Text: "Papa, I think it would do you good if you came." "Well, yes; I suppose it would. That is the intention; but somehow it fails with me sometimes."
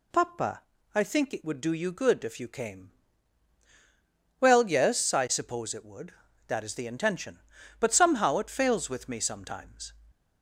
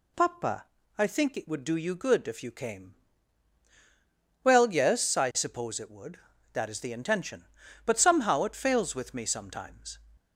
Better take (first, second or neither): neither